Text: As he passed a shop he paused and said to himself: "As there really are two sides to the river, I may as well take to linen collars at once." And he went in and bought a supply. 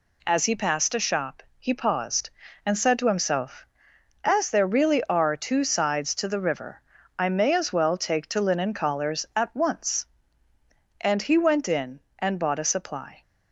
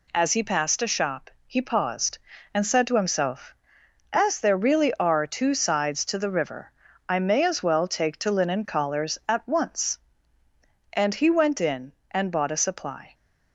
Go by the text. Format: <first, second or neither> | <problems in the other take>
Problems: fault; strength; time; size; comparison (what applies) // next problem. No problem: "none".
neither | pauses between "shop" and "he"; slight; the same in both